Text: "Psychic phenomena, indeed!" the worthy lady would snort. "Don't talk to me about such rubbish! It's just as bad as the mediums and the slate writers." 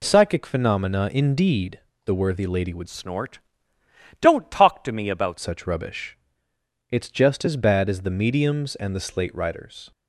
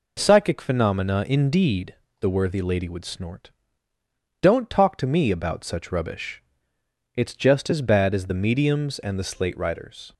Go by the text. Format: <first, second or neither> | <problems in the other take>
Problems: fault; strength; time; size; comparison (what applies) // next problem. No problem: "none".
second | changes voice from "snort" to "about"; from 2.8 to 5.3 s; 2.5 s long